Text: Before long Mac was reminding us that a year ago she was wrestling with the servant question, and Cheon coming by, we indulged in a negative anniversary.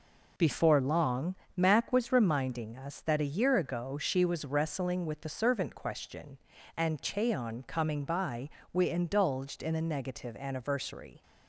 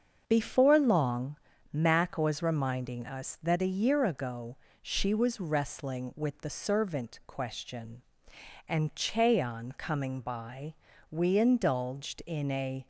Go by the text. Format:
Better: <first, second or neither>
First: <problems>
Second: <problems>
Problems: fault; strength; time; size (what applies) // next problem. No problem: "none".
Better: first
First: pauses between "long" and "Mac"; slight; at 1.3 s; 0.22 s long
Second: starts louder than the rest; until 1.2 s; 6.5 dB // pauses between "long" and "Mac"; slight; at 1.3 s; 0.34 s long // pauses between "ago" and "she"; slight; at 4.5 s; 0.24 s long // stops before "negative anniversary"; at 12.8 s